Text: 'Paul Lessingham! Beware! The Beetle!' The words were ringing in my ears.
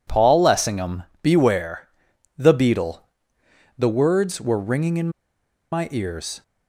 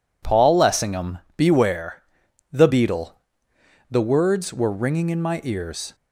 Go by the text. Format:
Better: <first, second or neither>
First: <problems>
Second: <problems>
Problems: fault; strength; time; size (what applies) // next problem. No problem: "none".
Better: second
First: pauses between "in" and "my"; noticeable; at 5.1 s; 0.61 s long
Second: none